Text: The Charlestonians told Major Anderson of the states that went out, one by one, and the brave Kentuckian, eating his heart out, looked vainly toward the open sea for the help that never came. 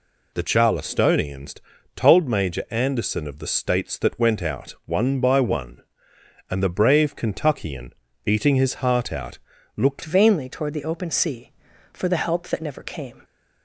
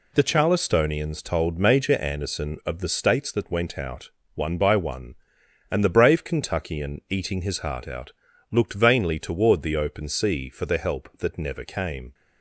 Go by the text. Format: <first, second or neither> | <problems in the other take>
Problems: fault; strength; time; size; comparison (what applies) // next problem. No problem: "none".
second | pauses between "Charlestonians" and "told"; at 1.5 s; 0.42 s long // changes voice at "vainly"; from 10.0 s on; 3.2 s long